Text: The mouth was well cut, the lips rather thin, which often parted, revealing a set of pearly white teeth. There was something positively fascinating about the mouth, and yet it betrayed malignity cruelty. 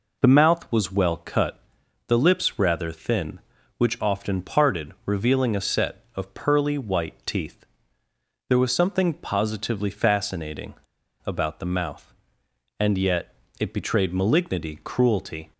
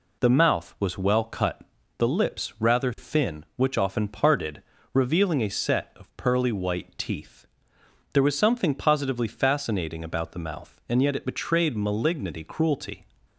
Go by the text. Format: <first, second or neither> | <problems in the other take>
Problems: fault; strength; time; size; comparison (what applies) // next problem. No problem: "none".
second | pauses between "fascinating" and "about"; noticeable; at 10.7 s; 0.50 s long // pauses between "yet" and "it"; slight; at 13.3 s; 0.26 s long